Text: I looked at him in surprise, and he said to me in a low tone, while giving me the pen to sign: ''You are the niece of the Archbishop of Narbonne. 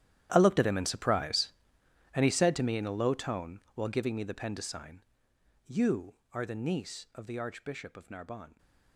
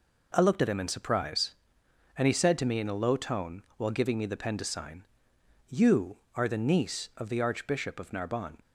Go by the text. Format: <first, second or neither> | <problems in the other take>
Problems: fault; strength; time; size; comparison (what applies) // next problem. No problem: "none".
second | gets quieter; strong; throughout; 17.5 dB